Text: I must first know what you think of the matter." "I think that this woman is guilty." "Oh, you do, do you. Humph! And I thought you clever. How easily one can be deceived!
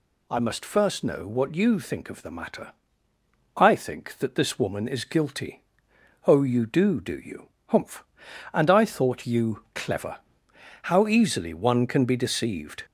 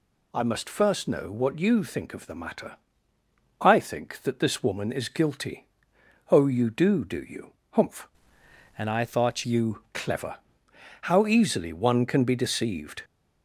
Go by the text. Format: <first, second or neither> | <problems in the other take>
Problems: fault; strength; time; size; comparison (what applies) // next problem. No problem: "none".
first | changes voice from "And" to "thought"; from 8.7 to 9.4 s; 0.7 s long